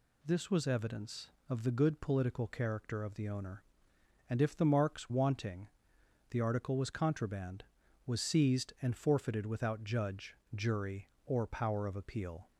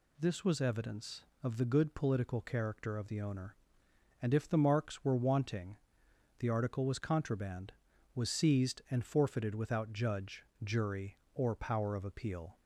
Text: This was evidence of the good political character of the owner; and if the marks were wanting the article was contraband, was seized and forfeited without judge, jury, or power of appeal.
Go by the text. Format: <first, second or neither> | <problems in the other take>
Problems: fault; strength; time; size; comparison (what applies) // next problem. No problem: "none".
second | skips "were"; at 5.1 s // pauses between "wanting" and "the"; noticeable; at 5.6 s; 0.62 s long; noticeable in the second